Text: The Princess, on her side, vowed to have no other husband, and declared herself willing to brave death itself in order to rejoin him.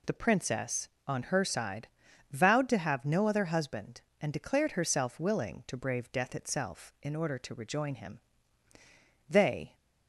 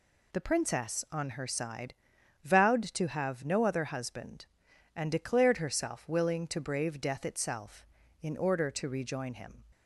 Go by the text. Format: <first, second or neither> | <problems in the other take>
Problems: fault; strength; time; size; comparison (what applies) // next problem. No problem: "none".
second | goes on to say "They"; slight; from 9.2 s on; 0.48 s long